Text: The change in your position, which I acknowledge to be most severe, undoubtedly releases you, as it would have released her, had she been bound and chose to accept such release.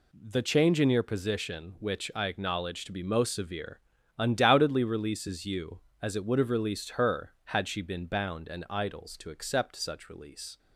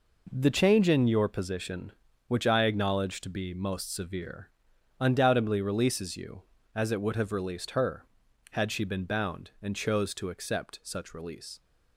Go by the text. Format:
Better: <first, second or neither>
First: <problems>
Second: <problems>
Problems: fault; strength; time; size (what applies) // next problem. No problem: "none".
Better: second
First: says "idols" for "chose"; at 8.7 s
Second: none